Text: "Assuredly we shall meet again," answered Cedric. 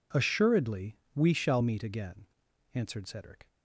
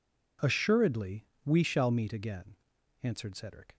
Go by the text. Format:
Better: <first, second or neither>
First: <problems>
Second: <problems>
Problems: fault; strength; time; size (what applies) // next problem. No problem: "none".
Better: neither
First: pauses between "Assuredly" and "we"; slight; at 0.9 s; 0.16 s long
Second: pauses between "Assuredly" and "we"; slight; at 1.2 s; 0.18 s long